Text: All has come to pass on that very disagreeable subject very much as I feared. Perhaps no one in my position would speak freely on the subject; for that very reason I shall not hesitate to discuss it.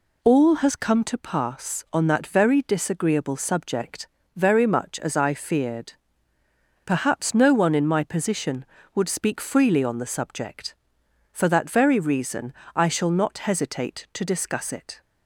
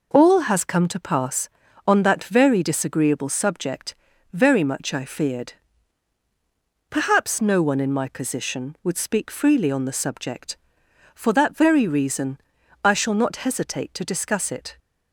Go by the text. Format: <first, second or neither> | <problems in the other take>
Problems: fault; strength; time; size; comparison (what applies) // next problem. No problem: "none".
first | pauses between "subject" and "very"; at 3.9 s; 0.38 s long; slight in the first // skips "as"; at 4.9 s // pauses between "reason" and "I"; at 12.3 s; 0.44 s long; slight in the first